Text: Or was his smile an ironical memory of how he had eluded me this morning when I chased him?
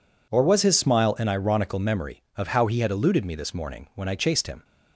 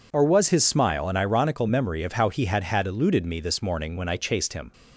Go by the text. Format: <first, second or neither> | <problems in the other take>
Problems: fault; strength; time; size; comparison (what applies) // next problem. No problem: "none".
first | says "had" twice; at 2.6 s